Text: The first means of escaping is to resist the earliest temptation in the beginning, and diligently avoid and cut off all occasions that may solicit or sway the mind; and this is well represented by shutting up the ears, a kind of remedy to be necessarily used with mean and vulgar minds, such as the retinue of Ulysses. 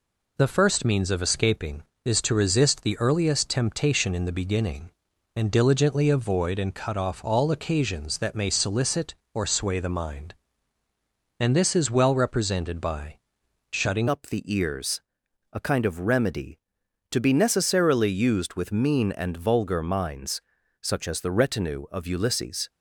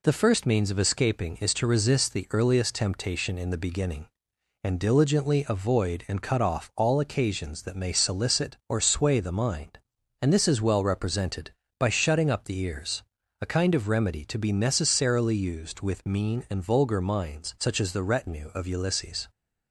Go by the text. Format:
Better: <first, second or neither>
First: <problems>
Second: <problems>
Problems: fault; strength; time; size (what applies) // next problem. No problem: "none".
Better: second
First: pauses between "by" and "shutting"; noticeable; at 13.1 s; 0.54 s long // changes voice at "up"; from 14.0 s on; 8.6 s long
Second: none